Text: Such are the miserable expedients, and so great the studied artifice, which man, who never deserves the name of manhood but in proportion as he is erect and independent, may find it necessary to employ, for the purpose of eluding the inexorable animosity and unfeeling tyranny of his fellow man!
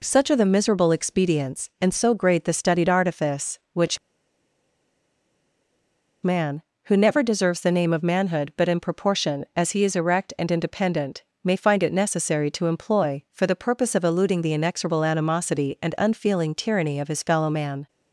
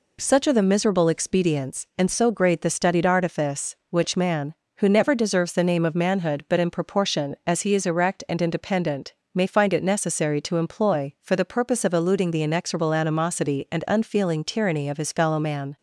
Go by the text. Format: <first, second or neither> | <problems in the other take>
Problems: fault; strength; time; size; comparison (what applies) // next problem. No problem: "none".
second | pauses between "which" and "man"; strong; at 3.9 s; 2.2 s long